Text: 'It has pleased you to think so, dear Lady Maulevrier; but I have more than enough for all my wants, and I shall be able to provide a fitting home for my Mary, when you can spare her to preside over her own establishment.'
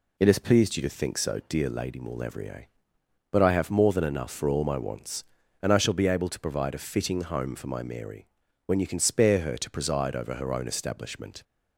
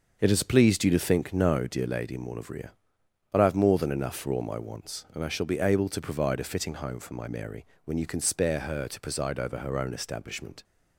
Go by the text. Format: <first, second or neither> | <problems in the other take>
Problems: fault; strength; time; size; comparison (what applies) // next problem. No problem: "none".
first | starts louder than the rest; until 1.2 s; 6 dB // says "no" for "so"; at 1.3 s